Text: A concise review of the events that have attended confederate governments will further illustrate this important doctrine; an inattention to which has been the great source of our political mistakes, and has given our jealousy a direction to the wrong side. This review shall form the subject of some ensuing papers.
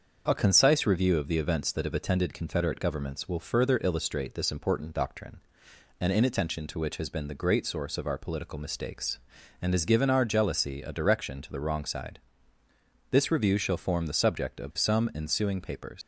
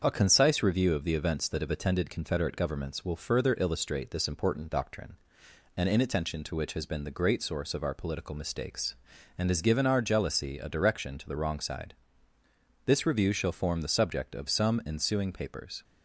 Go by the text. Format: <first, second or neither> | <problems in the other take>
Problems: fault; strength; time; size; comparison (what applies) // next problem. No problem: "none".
second | starts louder than the rest; until 1.2 s; 6.5 dB; also in the second // leaves "papers" unfinished; at 16.0 s; 105 ms